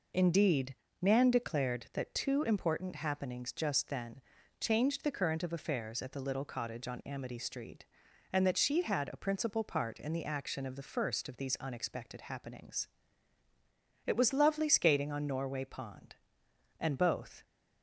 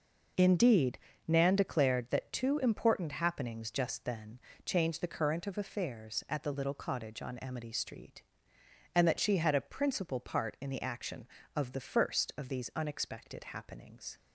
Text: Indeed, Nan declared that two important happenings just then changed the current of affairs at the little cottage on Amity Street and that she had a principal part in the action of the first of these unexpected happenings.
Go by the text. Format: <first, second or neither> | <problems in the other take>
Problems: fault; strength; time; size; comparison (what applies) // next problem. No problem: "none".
second | pauses between "then" and "changed"; at 4.1 s; 0.40 s long; slight in the second // goes on to say "It was lovely skating on Norway Pond and both"; strong; from 14.0 s on; 3.3 s long